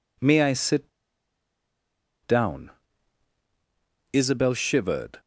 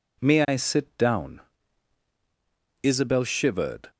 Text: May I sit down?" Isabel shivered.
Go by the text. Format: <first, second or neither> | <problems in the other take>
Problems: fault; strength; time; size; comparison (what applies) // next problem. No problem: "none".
second | pauses between "sit" and "down"; strong; at 0.8 s; 1.3 s long